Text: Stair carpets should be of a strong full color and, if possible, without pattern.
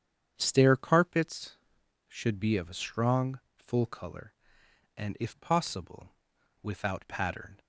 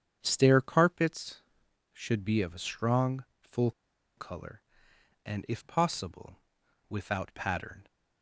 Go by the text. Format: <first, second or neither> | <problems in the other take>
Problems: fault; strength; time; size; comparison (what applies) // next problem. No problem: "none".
first | starts louder than the rest; strong; until 1.2 s; 8 dB; strong in the first // pauses between "strong" and "full"; slight; at 3.2 s; 0.16 s long; slight in the first // pauses between "full" and "color"; noticeable; at 3.7 s; 0.46 s long